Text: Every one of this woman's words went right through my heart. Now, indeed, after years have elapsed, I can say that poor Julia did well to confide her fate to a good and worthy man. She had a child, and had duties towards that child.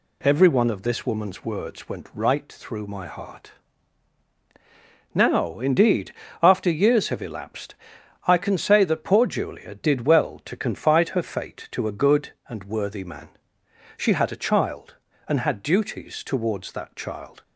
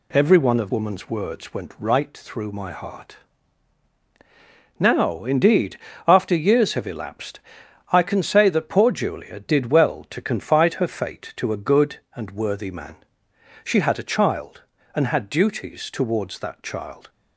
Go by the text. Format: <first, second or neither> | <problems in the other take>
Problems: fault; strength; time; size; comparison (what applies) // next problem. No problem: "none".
first | skips "this"; at 0.7 s